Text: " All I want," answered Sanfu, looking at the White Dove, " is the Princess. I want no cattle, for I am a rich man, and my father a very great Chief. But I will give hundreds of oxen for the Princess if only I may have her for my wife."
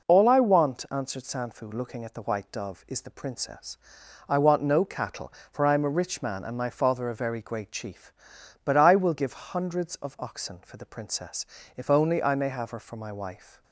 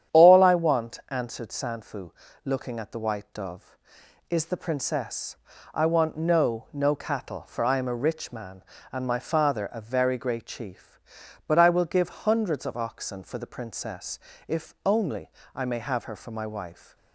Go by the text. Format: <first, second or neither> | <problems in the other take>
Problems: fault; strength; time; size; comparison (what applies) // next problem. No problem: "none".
first | starts louder than the rest; strong; until 1.2 s; 9.5 dB // says "no" twice; at 6.7 s // pauses between "Princess" and "if"; slight; at 14.1 s; 0.30 s long; slight in the first // pauses between "only" and "I"; slight; at 15.2 s; 0.24 s long